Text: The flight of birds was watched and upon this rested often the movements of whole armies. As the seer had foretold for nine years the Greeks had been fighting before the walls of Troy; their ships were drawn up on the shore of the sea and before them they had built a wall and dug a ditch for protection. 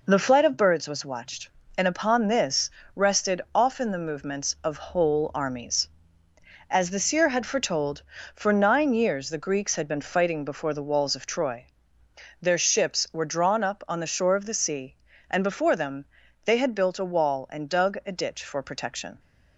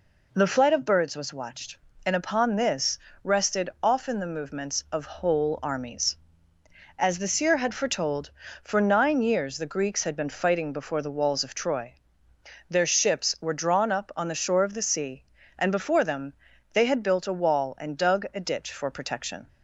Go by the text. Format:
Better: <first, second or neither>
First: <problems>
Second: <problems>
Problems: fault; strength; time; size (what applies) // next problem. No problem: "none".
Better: second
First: gets quieter; noticeable; throughout; 5.5 dB // pauses between "this" and "rested"; slight; at 2.7 s; 0.24 s long // pauses between "them" and "they"; at 16.0 s; 0.40 s long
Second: pauses between "this" and "rested"; slight; at 2.9 s; 0.24 s long // pauses between "them" and "they"; at 16.3 s; 0.40 s long